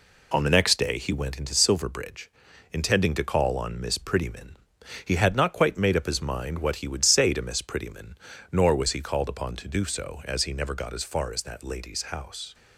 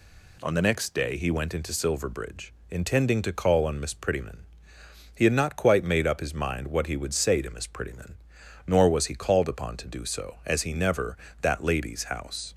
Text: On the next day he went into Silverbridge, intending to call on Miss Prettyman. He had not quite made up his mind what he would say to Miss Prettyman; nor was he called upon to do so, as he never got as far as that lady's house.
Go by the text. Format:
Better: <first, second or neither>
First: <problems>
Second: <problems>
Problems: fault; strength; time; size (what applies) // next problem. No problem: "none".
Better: first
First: none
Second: skips "got as far as"; at 11.2 s